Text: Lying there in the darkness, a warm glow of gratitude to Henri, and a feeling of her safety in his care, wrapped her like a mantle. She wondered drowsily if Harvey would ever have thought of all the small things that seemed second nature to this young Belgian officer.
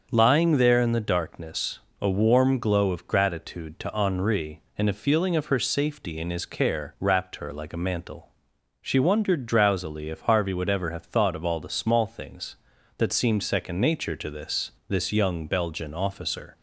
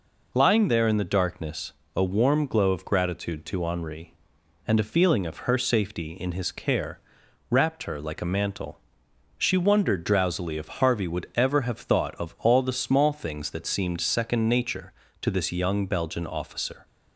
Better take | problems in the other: second | starts louder than the rest; until 1.1 s; 6.5 dB // says "this" twice; at 14.8 s

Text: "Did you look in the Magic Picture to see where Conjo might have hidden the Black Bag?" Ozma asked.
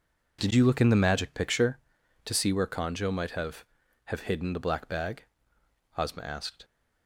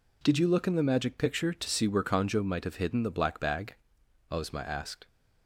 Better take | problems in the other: second | says "have" twice; at 4.0 s

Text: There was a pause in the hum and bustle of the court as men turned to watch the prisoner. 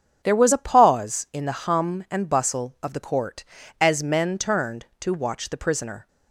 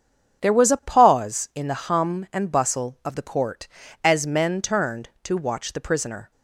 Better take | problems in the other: neither | starts louder than the rest; strong; the same in both

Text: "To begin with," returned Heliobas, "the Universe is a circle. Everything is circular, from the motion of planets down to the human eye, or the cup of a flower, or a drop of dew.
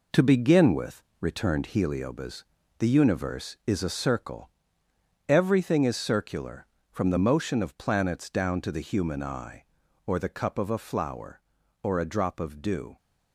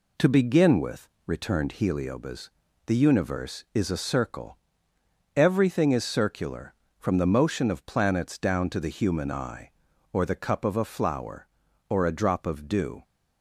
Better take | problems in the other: second | gets quieter; strong; throughout; 7.5 dB

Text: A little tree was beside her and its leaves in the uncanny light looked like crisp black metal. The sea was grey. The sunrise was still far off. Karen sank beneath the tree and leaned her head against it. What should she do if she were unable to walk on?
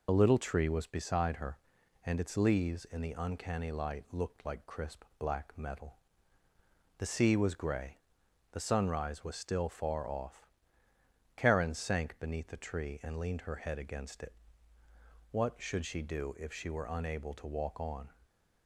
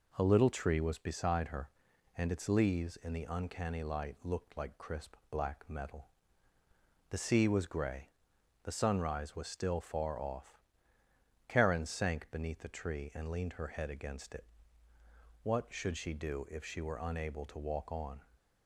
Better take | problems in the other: second | loses the start of "A"; at 0.0 s; 65 ms // pauses between "crisp" and "black"; slight; at 5.0 s; 0.16 s long; slight in the second

